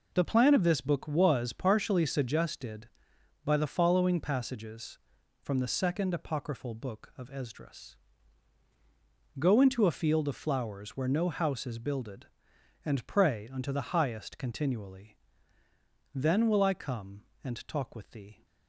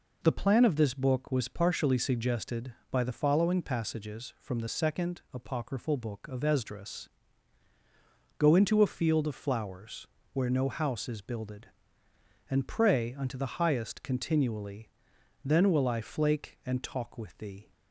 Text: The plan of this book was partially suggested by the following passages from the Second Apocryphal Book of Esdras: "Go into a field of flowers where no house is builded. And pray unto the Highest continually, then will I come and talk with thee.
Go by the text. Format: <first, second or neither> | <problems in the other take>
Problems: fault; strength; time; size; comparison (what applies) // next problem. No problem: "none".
first | pauses between "flowers" and "where"; slight; at 10.0 s; 0.26 s long // says "flake" for "come"; at 16.0 s